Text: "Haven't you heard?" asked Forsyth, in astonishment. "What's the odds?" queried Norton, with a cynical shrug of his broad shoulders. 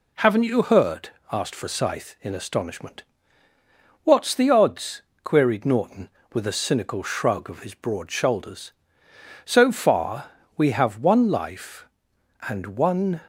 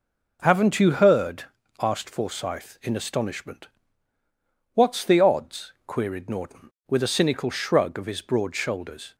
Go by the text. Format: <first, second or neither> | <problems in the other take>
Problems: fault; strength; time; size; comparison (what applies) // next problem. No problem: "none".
second | goes on to say "So far we have one life and one"; strong; from 9.4 s on; 3.7 s long